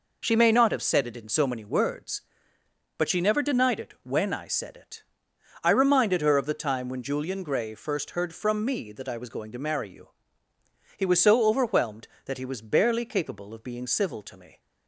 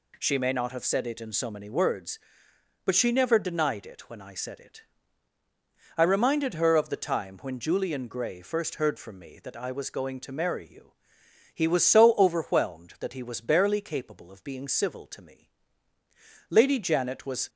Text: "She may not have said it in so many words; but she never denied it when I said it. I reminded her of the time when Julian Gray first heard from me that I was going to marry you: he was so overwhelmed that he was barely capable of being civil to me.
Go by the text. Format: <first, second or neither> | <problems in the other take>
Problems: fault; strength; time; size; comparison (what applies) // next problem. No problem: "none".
first | goes on to say "Lady Janet was"; noticeable; from 16.4 s on; 1.0 s long